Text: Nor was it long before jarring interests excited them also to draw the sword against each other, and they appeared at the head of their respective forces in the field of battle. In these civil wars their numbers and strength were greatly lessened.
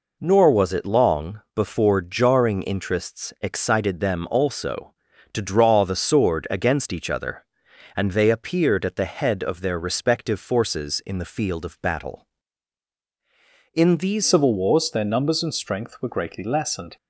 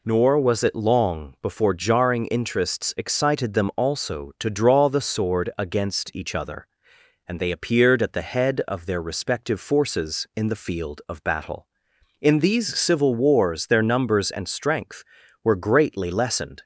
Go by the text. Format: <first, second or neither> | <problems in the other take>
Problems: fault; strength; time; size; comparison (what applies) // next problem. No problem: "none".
second | changes voice at "civil"; from 14.2 s on; 2.7 s long